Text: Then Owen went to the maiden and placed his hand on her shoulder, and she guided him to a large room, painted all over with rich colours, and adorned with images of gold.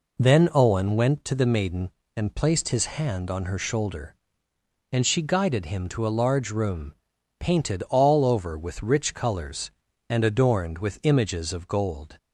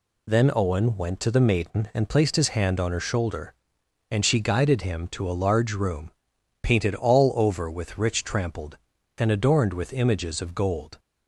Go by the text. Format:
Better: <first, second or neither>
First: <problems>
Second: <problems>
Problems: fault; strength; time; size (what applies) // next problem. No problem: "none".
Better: first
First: none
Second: says "trampled" for "colours"; at 8.2 s